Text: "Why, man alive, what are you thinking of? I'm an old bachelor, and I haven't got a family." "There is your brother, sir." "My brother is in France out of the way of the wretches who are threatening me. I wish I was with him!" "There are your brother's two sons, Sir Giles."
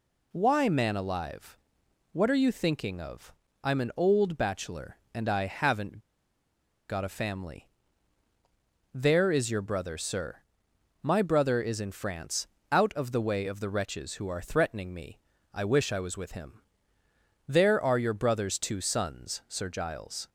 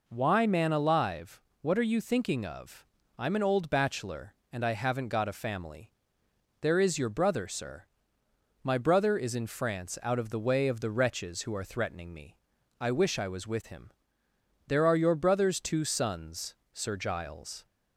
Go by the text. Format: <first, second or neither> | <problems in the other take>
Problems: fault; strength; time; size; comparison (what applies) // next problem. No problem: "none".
second | pauses between "haven't" and "got"; noticeable; at 5.9 s; 0.90 s long // pauses between "France" and "out"; slight; at 12.4 s; 0.22 s long